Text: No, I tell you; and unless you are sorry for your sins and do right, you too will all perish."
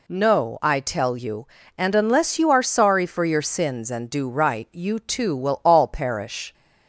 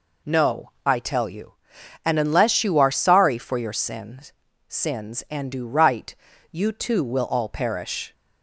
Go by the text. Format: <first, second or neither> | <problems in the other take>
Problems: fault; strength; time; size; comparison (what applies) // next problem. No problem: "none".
first | says "sins" twice; at 4.6 s